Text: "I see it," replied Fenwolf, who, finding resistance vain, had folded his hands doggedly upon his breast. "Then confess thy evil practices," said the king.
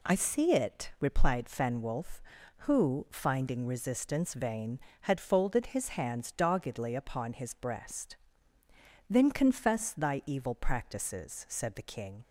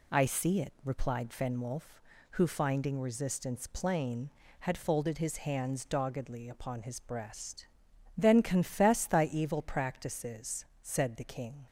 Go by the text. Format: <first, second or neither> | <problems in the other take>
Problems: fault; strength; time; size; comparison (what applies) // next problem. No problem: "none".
first | says "plain" for "vain"; at 3.6 s